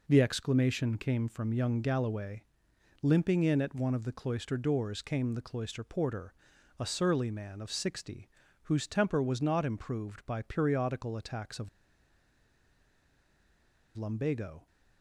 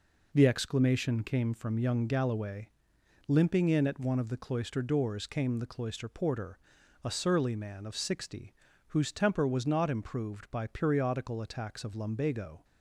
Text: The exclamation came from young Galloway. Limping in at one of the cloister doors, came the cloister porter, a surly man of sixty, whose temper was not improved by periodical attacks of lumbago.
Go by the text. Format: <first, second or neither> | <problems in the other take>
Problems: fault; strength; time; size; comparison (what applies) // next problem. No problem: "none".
second | pauses between "of" and "lumbago"; strong; at 11.6 s; 2.2 s long